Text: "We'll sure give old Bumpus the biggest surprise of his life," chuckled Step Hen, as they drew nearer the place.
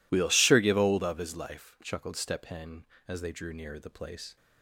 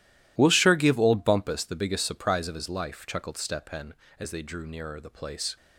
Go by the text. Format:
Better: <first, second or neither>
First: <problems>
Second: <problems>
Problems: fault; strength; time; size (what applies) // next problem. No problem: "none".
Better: second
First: skips "Bumpus the biggest surprise"; at 1.0 s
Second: none